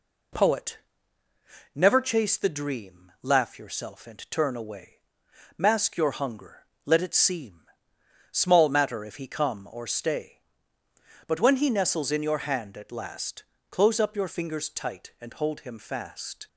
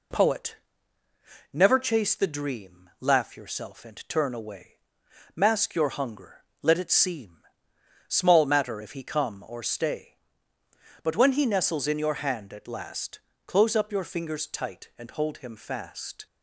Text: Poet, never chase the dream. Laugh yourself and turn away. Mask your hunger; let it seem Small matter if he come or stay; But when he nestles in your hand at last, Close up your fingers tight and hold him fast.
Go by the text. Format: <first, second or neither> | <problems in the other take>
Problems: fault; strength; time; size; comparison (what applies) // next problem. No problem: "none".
neither | pauses between "seem" and "Small"; noticeable; the same in both